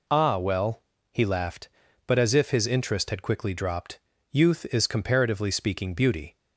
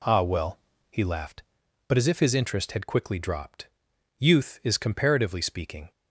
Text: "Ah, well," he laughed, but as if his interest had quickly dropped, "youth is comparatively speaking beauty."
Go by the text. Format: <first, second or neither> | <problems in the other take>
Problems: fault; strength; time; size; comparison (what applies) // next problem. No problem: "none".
first | stops before "beauty"; at 5.9 s